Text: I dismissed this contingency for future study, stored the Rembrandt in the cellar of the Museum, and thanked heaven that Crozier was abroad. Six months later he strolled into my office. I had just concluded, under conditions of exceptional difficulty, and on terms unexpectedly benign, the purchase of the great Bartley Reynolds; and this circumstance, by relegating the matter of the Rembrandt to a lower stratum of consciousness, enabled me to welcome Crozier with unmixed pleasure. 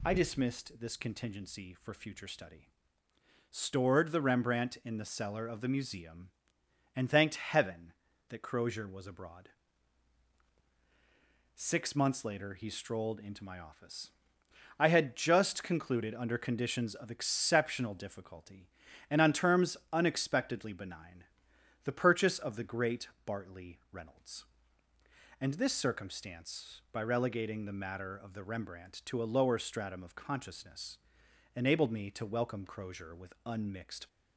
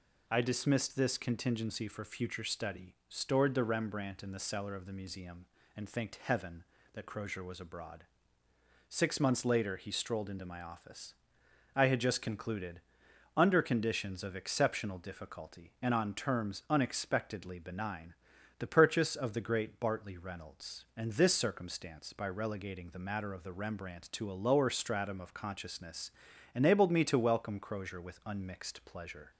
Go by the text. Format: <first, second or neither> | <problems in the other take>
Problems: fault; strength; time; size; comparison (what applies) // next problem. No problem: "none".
second | pauses between "terms" and "unexpectedly"; slight; at 19.7 s; 0.16 s long // pauses between "great" and "Bartley"; slight; at 23.0 s; 0.16 s long // stops before "pleasure"; at 34.0 s